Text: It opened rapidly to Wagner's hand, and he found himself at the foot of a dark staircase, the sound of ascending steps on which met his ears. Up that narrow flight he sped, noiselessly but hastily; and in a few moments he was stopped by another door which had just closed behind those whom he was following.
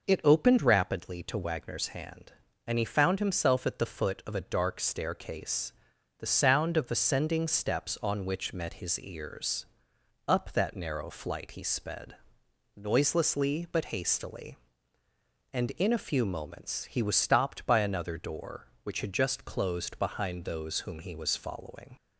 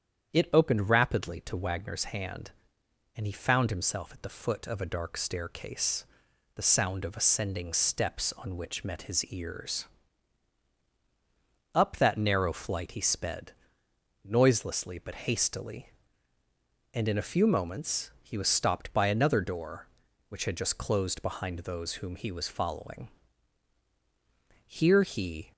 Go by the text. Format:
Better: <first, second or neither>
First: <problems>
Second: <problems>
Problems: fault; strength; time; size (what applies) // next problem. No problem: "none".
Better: first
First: none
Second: starts louder than the rest; strong; until 1.3 s; 8.5 dB // goes on to say "Here he"; noticeable; from 24.6 s on; 0.86 s long